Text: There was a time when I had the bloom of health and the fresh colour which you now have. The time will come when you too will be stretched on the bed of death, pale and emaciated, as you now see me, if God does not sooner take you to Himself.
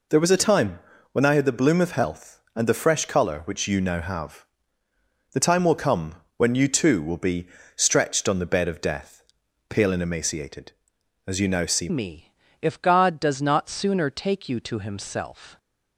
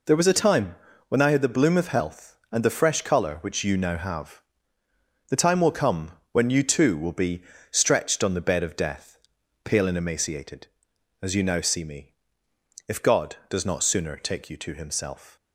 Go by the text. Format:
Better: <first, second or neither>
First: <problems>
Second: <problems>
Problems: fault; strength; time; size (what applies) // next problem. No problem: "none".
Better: second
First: pauses between "time" and "when"; slight; at 0.8 s; 0.32 s long // pauses between "come" and "when"; slight; at 6.1 s; 0.20 s long // pauses between "be" and "stretched"; slight; at 7.4 s; 0.28 s long // changes voice at "me"; from 11.8 s on; 3.7 s long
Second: pauses between "time" and "when"; slight; at 0.7 s; 0.32 s long // pauses between "come" and "when"; slight; at 6.1 s; 0.18 s long // pauses between "be" and "stretched"; slight; at 7.4 s; 0.28 s long